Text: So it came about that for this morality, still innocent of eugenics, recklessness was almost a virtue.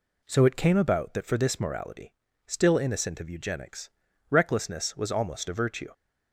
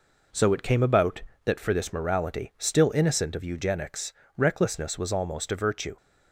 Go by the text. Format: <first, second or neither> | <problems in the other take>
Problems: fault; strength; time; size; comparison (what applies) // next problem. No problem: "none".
neither | none